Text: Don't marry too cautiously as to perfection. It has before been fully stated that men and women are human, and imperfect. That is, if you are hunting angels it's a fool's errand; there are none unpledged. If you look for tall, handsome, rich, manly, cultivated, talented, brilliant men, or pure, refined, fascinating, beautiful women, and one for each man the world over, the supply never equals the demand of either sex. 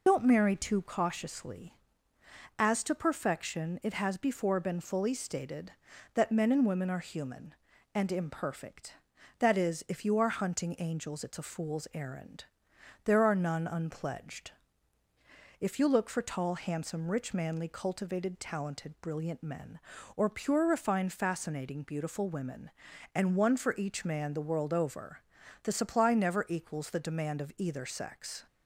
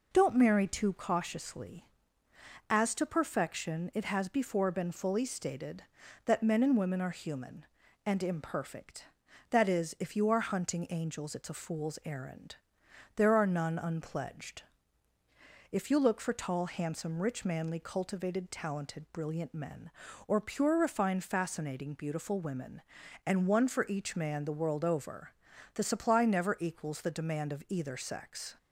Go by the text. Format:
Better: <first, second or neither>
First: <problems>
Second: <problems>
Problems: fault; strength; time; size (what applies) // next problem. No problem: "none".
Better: second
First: loses the start of "Don't"; at 0.0 s; 45 ms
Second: none